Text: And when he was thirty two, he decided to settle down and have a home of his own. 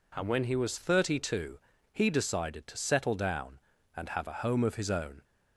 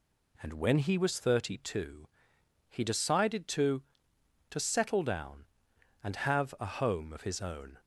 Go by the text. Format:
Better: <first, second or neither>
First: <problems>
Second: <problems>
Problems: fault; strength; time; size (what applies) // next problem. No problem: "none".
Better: first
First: none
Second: says "to" twice; at 4.4 s